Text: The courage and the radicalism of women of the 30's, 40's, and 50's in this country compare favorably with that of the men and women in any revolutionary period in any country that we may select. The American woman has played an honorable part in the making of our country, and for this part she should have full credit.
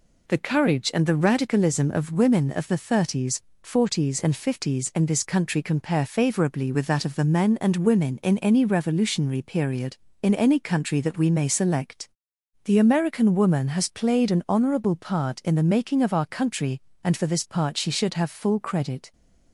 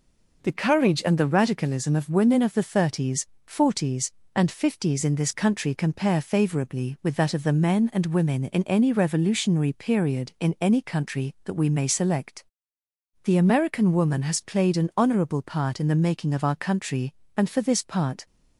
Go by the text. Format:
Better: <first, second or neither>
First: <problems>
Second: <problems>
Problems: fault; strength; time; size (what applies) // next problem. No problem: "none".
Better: first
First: none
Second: stops before "she should have full credit"; at 18.2 s